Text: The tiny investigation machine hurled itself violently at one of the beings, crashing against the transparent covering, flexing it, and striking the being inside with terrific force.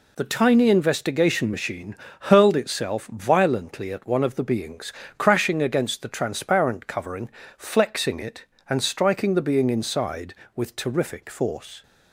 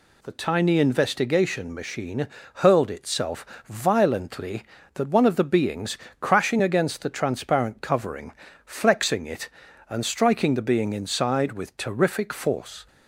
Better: first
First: pauses between "machine" and "hurled"; slight; at 1.9 s; 0.26 s long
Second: pauses between "machine" and "hurled"; slight; at 2.2 s; 0.30 s long // pauses between "itself" and "violently"; slight; at 3.4 s; 0.22 s long // says "that" for "at"; at 4.9 s

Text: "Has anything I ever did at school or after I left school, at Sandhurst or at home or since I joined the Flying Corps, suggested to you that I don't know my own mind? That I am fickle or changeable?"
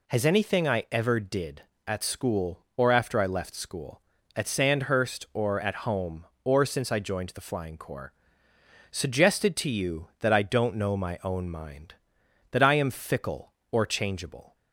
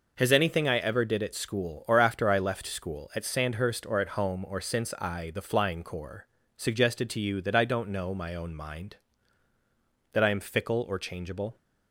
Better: first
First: none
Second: skips "joined"; at 5.3 s

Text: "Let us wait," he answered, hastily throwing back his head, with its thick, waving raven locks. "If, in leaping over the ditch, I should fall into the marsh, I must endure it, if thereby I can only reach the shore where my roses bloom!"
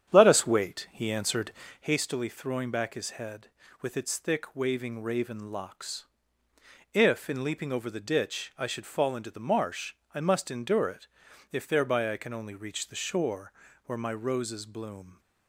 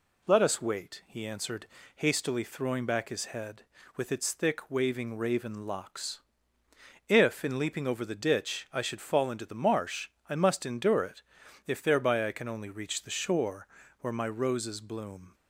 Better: second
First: starts louder than the rest; strong; until 1.9 s; 9 dB // pauses between "shore" and "where"; slight; at 13.5 s; 0.32 s long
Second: pauses between "shore" and "where"; slight; at 13.6 s; 0.32 s long

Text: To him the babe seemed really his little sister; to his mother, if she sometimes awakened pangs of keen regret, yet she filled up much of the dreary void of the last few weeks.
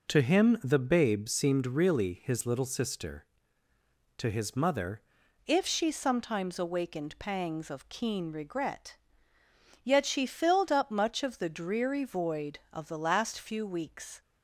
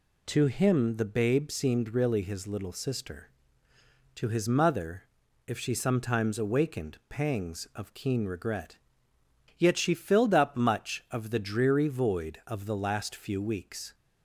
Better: second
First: changes voice at "if"; from 5.4 s on; 8.8 s long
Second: none

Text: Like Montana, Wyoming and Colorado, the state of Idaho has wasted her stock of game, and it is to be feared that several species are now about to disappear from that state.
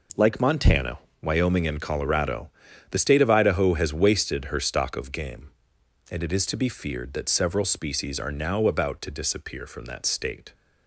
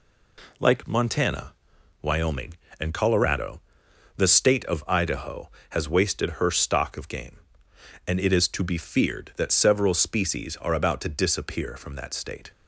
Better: first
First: none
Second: skips "now"; at 10.7 s

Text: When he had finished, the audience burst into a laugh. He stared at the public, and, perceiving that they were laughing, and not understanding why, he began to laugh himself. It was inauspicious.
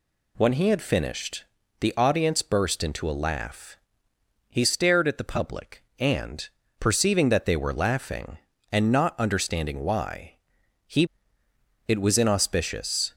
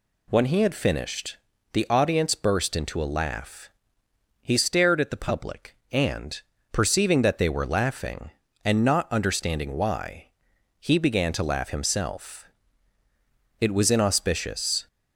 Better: second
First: skips "began to laugh himself"; at 11.4 s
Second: none

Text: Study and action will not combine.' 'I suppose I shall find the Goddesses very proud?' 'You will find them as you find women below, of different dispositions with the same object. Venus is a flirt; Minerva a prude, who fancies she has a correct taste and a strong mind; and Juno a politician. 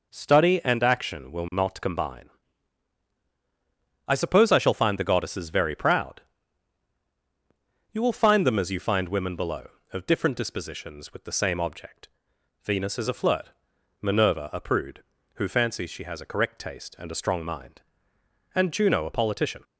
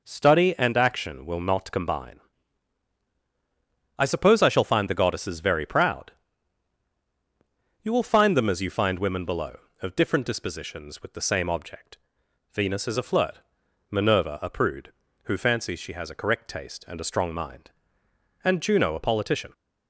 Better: neither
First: none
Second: none

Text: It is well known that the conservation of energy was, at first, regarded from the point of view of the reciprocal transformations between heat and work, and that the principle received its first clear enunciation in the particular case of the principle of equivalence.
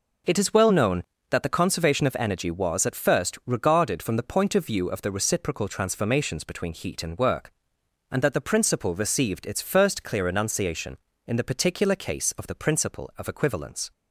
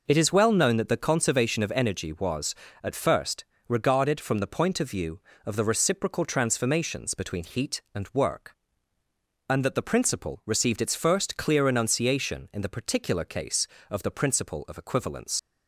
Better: first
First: none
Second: leaves "equivalence" unfinished; at 15.3 s; 80 ms

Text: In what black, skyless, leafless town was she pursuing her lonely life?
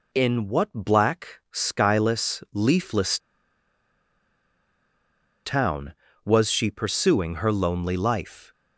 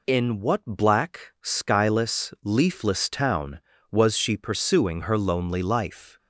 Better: second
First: pauses between "leafless" and "town"; strong; at 3.1 s; 2.2 s long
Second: none

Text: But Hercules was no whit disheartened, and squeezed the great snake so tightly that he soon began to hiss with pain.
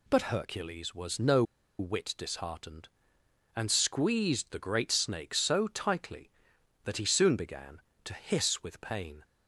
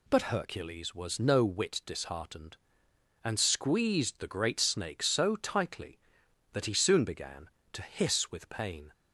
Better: second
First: pauses between "no" and "whit"; slight; at 1.4 s; 0.36 s long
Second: none

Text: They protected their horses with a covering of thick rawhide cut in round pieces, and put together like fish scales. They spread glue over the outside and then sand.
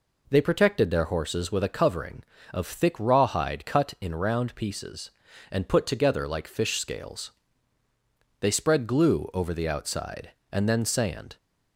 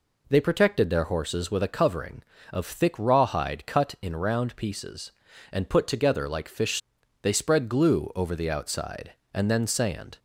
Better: first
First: none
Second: skips "scales"; at 7.0 s

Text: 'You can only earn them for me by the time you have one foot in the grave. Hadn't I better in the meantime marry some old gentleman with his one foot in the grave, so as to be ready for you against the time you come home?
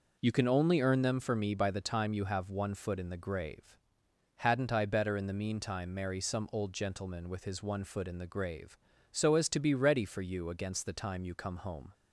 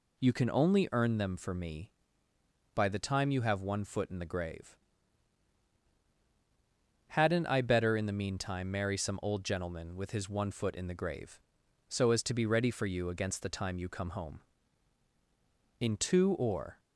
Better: first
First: none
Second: goes on to say "In two or"; noticeable; from 15.7 s on; 1.0 s long

